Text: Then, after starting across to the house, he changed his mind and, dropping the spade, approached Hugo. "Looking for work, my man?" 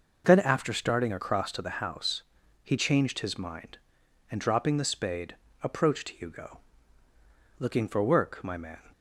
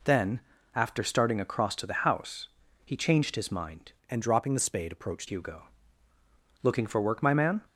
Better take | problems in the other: first | changes voice from "and" to "approached"; from 4.0 to 5.2 s; 1.2 s long

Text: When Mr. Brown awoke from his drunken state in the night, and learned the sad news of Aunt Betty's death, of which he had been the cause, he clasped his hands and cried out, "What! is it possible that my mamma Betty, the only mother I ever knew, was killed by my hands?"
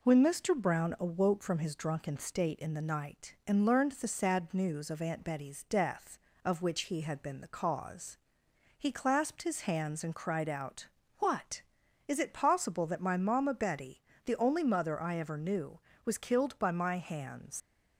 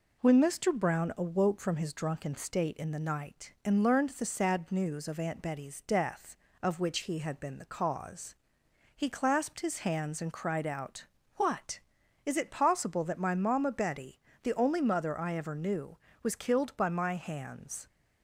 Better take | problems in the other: second | leaves "hands" unfinished; at 17.6 s; 85 ms

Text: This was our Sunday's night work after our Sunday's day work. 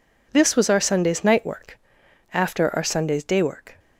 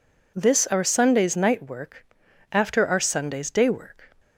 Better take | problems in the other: first | skips "was"; at 0.6 s // pauses between "work" and "after"; noticeable; at 2.0 s; 0.48 s long; noticeable in the first

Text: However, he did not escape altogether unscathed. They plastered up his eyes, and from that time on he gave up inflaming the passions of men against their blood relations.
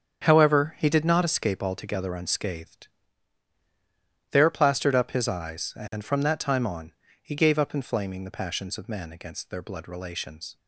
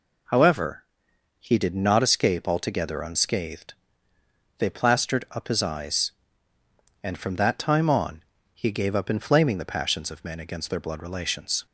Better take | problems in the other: second | starts louder than the rest; strong; until 1.2 s; 8 dB // says "There" for "They"; at 4.2 s // pauses between "on" and "he"; slight; at 6.9 s; 0.30 s long; slight in the second

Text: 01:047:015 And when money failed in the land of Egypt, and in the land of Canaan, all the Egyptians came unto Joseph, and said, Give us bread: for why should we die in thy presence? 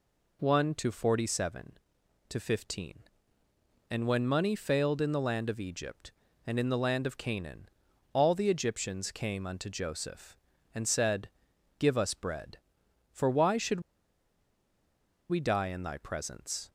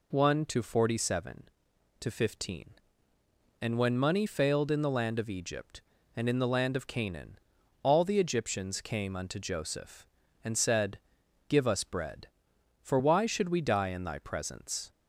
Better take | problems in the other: second | pauses between "should" and "we"; strong; at 13.8 s; 1.4 s long

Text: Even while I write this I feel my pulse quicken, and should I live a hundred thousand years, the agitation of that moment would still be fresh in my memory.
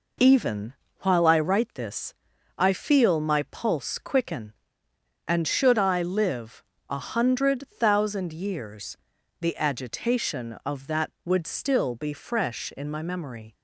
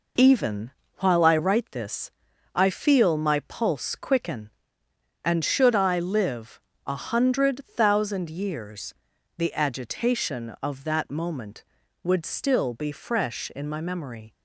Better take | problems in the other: second | pauses between "Even" and "while"; slight; at 0.7 s; 0.28 s long; slight in the second // pauses between "this" and "I"; at 2.1 s; 0.44 s long; also in the second // pauses between "live" and "a"; slight; at 6.6 s; 0.28 s long; slight in the second // skips "moment"; at 11.1 s

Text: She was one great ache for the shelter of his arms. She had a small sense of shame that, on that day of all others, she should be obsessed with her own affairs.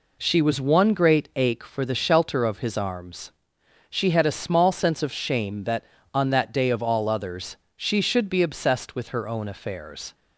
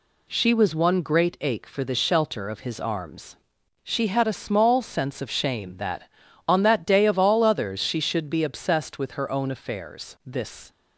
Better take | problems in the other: first | goes on to say "This"; slight; from 10.2 s on; 0.44 s long

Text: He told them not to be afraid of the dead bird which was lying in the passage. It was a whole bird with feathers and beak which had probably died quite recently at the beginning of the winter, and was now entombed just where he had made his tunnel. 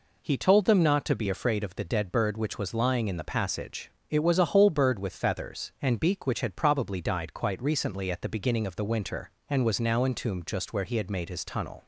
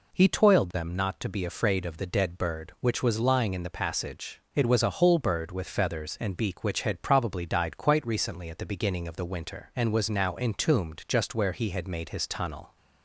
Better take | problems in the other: first | says "toiled" for "told"; at 0.2 s

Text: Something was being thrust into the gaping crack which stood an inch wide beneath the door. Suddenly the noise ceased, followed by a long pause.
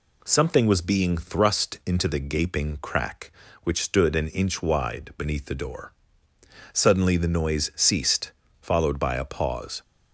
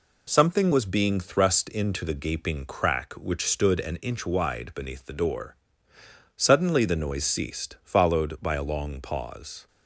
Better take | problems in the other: second | skips "long"; at 9.2 s

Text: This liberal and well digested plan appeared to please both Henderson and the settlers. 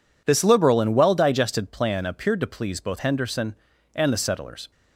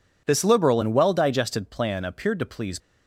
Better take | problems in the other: first | stops before "both Henderson and the settlers"; at 2.7 s

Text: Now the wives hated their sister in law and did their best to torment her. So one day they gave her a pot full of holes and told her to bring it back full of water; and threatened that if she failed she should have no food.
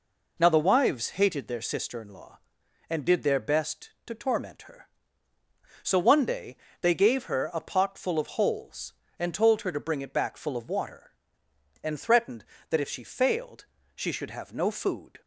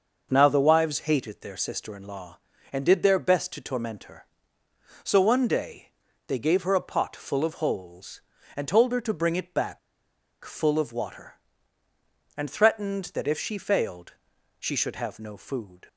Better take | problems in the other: first | pauses between "day" and "they"; at 5.8 s; 0.40 s long; slight in the first // pauses between "back" and "full"; noticeable; at 9.7 s; 0.64 s long // pauses between "failed" and "she"; noticeable; at 14.1 s; 0.48 s long; slight in the first

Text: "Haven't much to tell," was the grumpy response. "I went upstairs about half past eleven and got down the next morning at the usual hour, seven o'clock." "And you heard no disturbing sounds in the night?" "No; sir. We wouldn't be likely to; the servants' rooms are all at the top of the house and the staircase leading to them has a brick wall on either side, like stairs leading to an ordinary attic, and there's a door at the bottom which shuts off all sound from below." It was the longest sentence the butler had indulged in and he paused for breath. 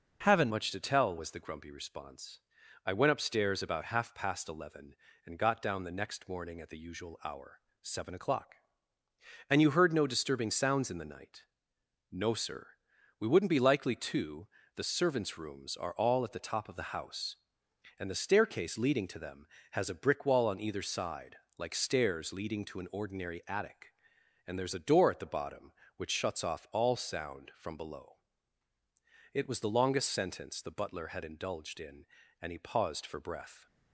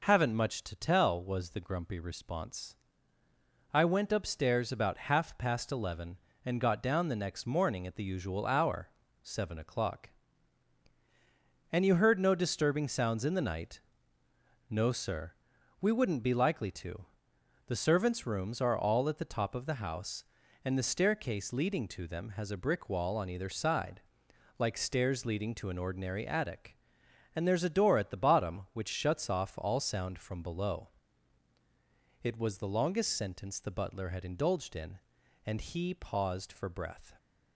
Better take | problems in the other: second | changes voice at "much"; from 0.5 s on; 33.1 s long

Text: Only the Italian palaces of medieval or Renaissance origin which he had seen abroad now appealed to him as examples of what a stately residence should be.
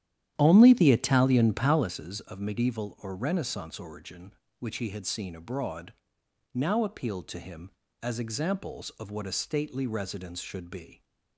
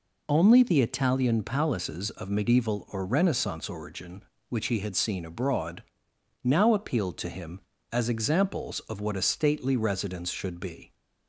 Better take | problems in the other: second | starts louder than the rest; strong; until 1.9 s; 11 dB // pauses between "abroad" and "now"; noticeable; at 5.9 s; 0.60 s long; noticeable in the second

